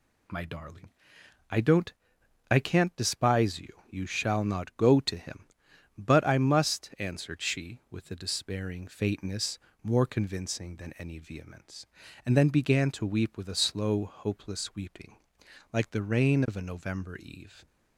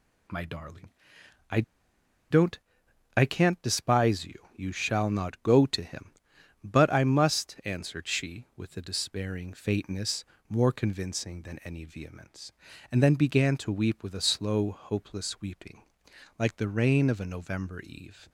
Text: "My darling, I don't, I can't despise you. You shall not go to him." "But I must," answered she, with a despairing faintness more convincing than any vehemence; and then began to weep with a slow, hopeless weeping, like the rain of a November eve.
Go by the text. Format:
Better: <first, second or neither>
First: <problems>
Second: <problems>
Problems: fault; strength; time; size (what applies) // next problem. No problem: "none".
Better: first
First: pauses between "faintness" and "more"; slight; at 9.5 s; 0.24 s long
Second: pauses between "I" and "don't"; noticeable; at 1.6 s; 0.68 s long // pauses between "faintness" and "more"; slight; at 10.2 s; 0.24 s long